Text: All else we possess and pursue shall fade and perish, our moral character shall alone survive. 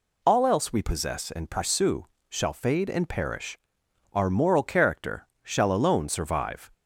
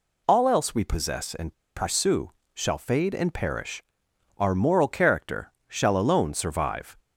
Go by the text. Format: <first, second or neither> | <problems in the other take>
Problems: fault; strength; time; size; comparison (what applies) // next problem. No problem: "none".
first | pauses between "and" and "pursue"; slight; at 1.5 s; 0.23 s long // pauses between "pursue" and "shall"; slight; at 2.2 s; 0.24 s long; slight in the first // pauses between "character" and "shall"; slight; at 5.5 s; 0.16 s long; slight in the first